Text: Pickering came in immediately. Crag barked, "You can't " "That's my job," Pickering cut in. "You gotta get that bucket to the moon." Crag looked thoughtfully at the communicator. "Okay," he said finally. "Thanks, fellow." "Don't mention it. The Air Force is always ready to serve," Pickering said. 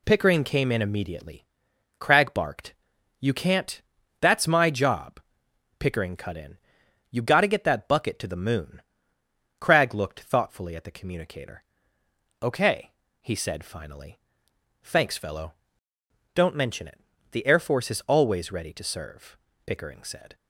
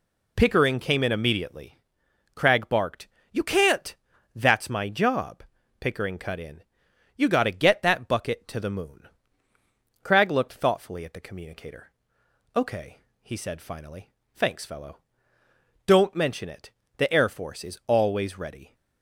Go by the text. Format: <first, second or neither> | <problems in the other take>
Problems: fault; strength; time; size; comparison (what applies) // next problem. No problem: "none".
first | stops before "to serve Pickering said"; at 18.7 s